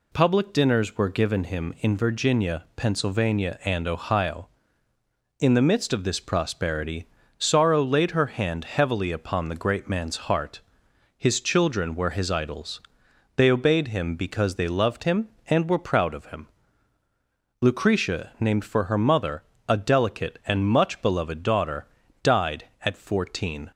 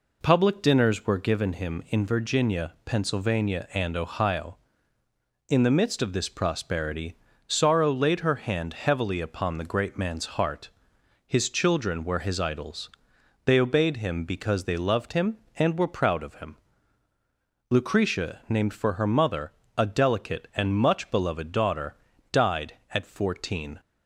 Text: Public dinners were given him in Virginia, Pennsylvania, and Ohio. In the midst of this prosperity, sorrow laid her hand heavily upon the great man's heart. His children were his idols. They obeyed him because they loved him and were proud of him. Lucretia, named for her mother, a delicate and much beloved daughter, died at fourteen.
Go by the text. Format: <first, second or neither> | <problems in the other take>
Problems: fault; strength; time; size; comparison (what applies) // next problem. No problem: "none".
first | starts louder than the rest; until 1.2 s; 4 dB